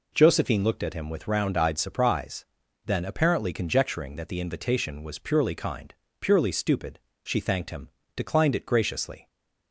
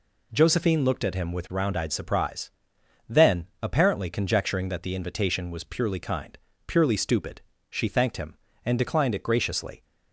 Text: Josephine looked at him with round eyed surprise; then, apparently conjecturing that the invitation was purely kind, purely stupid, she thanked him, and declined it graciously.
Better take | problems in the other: second | skips "and"; at 8.0 s

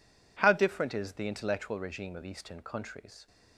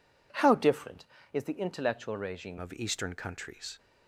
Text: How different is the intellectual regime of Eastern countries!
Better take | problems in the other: first | changes voice at "of"; from 2.5 s on; 1.2 s long

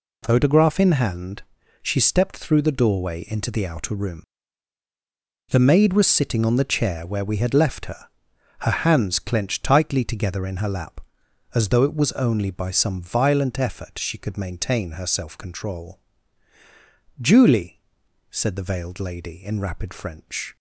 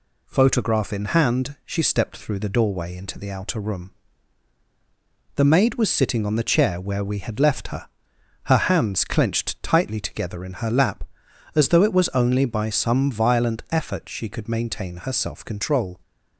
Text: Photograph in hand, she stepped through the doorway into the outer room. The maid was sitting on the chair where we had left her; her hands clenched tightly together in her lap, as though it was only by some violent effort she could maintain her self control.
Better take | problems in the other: second | goes on to say "Julie said the veiled lady in rapid French"; strong; from 17.1 s on; 3.3 s long

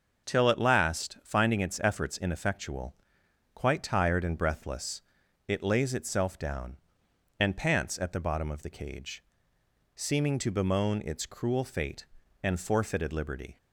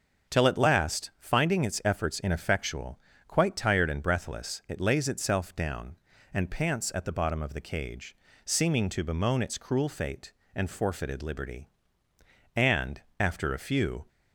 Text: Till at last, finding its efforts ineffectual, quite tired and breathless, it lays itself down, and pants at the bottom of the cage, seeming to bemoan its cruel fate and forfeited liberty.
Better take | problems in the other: first | starts louder than the rest; until 1.3 s; 6.5 dB; also in the first // goes on to say "And after a few"; from 12.5 s on; 1.5 s long

